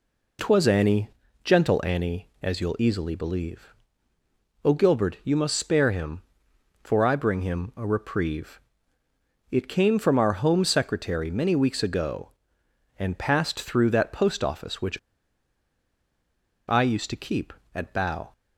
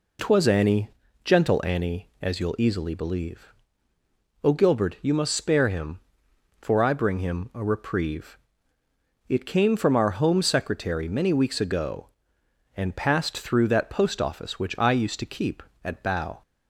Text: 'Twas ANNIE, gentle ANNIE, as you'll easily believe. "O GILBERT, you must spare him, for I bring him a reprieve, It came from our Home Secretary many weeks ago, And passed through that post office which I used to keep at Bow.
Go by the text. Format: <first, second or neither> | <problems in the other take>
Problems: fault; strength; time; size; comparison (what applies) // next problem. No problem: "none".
second | pauses between "which" and "I"; strong; at 14.9 s; 1.7 s long